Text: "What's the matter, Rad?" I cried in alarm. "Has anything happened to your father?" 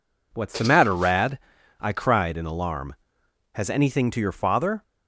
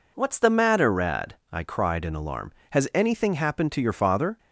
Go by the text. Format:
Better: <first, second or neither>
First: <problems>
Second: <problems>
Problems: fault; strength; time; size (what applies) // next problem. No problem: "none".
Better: second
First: skips "happened"; at 4.1 s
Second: none